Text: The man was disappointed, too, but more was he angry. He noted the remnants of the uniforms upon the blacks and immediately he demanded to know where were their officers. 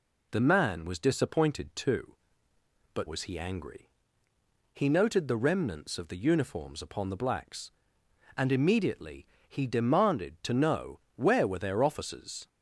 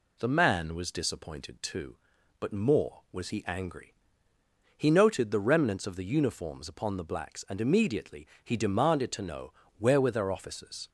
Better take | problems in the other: second | skips "more"; at 3.0 s // pauses between "immediately" and "he"; slight; at 9.2 s; 0.22 s long; slight in the second // pauses between "know" and "where"; slight; at 10.9 s; 0.16 s long; slight in the second

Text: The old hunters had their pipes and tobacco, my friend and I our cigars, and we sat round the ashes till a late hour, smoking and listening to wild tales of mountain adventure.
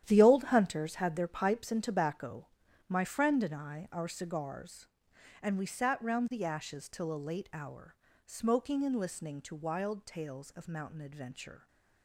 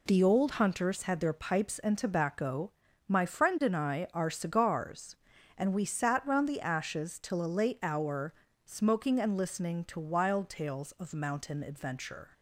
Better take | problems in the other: second | gets quieter; strong; throughout; 12 dB

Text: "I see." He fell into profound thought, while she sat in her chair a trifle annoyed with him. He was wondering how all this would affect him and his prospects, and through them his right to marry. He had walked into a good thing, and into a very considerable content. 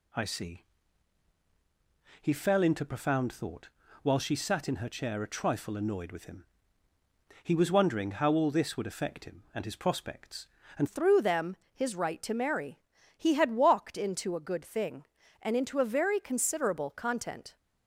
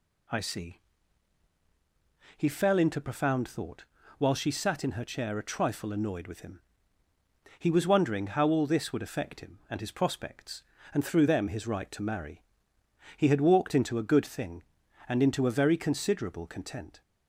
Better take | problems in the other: second | changes voice at "through"; from 10.8 s on; 6.7 s long // pauses between "them" and "his"; slight; at 11.5 s; 0.18 s long

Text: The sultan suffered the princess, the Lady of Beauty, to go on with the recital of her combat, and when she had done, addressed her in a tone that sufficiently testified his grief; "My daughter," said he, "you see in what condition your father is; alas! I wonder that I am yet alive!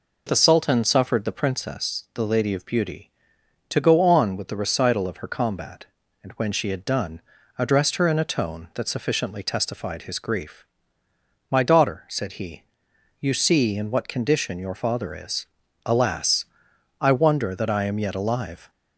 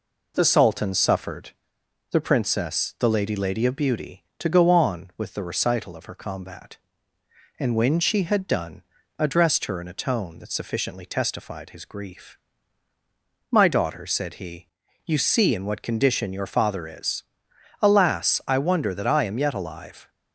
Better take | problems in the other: first | pauses between "suffered" and "the"; noticeable; at 1.5 s; 0.60 s long // says "Lady" twice; at 3.3 s

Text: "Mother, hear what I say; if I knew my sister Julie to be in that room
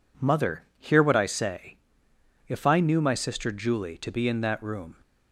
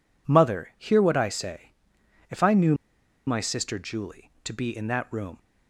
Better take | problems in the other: first | pauses between "knew" and "my"; noticeable; at 2.7 s; 0.53 s long

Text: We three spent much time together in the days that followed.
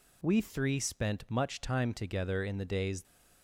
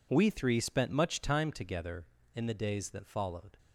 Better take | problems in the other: second | stops before "that followed"; at 3.0 s

